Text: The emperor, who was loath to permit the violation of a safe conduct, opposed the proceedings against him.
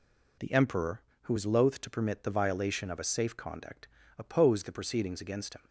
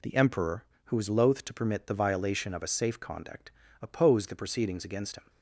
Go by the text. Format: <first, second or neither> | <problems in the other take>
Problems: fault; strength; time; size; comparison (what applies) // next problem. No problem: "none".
neither | none